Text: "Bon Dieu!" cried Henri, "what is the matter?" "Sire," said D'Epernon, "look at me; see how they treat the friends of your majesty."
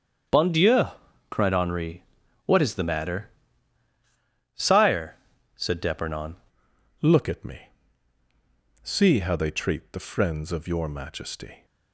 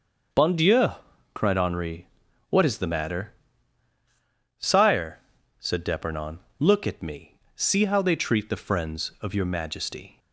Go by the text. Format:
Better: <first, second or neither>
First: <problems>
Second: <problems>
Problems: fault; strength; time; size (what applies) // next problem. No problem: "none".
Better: second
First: starts louder than the rest; strong; until 1.7 s; 7.5 dB // changes voice at "look"; from 7.0 s on; 4.6 s long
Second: starts louder than the rest; noticeable; until 1.7 s; 6 dB